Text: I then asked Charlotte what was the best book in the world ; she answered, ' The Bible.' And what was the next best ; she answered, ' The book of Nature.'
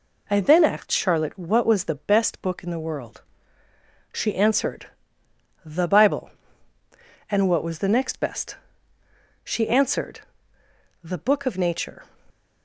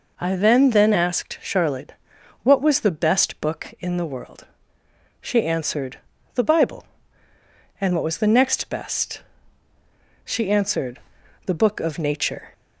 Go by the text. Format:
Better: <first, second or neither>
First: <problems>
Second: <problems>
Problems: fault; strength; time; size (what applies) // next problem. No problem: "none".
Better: first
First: none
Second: says "then" twice; at 0.6 s // pauses between "Charlotte" and "what"; noticeable; at 1.9 s; 0.50 s long